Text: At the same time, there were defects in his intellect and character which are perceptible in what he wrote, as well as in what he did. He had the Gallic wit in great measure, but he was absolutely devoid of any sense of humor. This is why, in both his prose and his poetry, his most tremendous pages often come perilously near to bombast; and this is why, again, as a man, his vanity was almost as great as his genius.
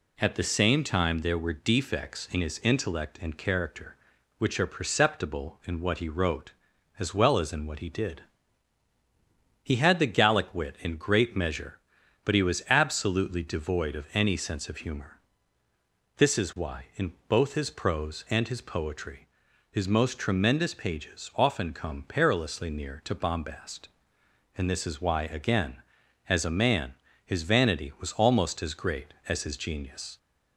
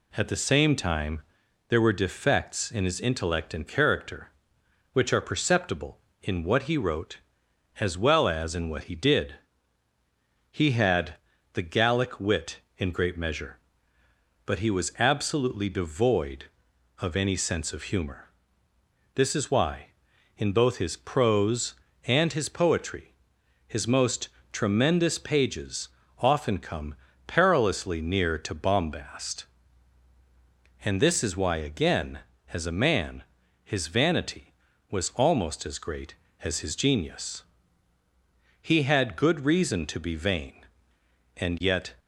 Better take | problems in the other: first | pauses between "had" and "the"; at 11.1 s; 0.40 s long // pauses between "most" and "tremendous"; slight; at 24.2 s; 0.24 s long // pauses between "pages" and "often"; slight; at 25.8 s; 0.30 s long // pauses between "come" and "perilously"; slight; at 26.9 s; 0.30 s long // goes on to say "He had good reason to be vain and yet"; strong; from 38.5 s on; 3.3 s long

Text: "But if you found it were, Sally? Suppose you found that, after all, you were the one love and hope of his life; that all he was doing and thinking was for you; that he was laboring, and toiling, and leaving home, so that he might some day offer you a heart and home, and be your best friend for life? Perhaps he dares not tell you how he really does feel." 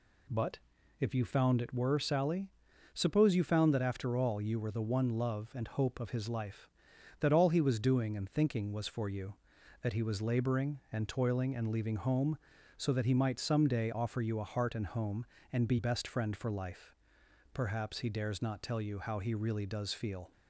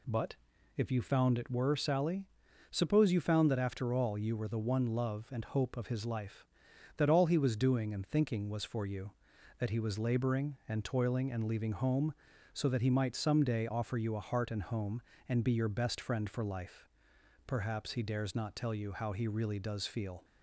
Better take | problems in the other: second | pauses between "But" and "if"; at 0.5 s; 0.42 s long; also in the second // skips "your"; at 15.7 s

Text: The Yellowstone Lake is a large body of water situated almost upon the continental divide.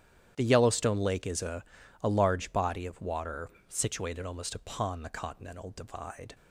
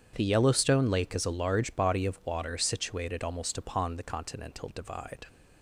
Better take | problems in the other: second | starts louder than the rest; strong; until 1.3 s; 10.5 dB; strong in the second // says "a" twice; at 2.0 s // pauses between "water" and "situated"; slight; at 3.5 s; 0.18 s long

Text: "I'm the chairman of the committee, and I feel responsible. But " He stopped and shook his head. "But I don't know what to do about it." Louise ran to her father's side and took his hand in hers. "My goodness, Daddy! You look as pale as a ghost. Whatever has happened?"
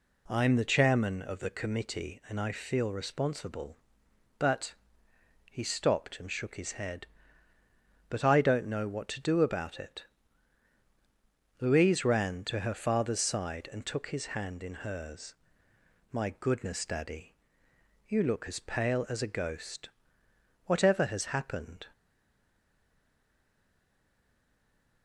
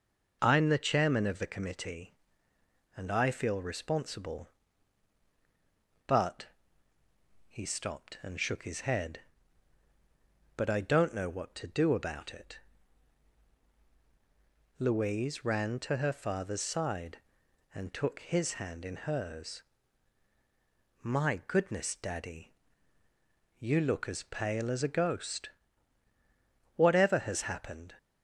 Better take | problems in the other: second | stays silent after the last word; strong; from 21.9 s on; 3.1 s long

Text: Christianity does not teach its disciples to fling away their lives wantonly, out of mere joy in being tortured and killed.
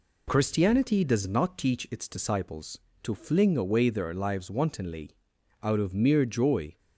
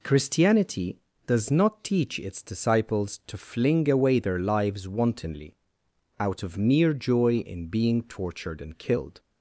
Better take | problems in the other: second | stops before "in being tortured and killed"; at 6.7 s

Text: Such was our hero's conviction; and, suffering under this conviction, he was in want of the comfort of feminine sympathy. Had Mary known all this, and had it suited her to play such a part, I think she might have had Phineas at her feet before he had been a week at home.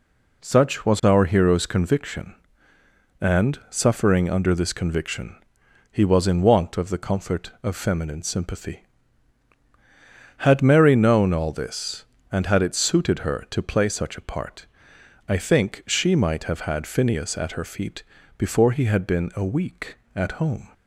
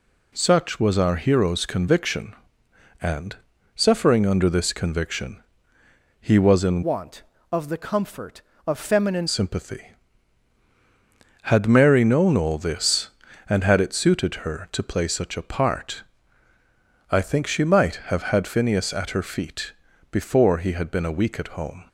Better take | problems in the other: first | changes voice from "want" to "feminine"; from 6.8 to 9.2 s; 2.4 s long // pauses between "feet" and "before"; at 19.7 s; 0.40 s long; slight in the first

